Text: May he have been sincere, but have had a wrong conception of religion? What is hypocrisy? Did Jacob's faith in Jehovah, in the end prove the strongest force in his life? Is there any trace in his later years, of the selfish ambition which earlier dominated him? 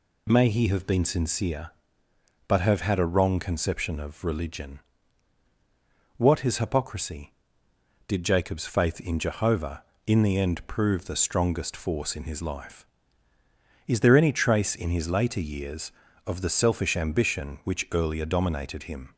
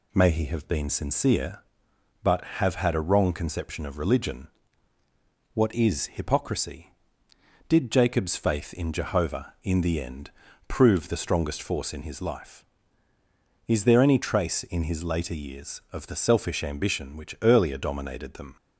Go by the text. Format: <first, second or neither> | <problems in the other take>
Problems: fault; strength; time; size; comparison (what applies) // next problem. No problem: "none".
first | pauses between "end" and "prove"; slight; at 10.3 s; 0.34 s long // says "them" for "him"; at 18.3 s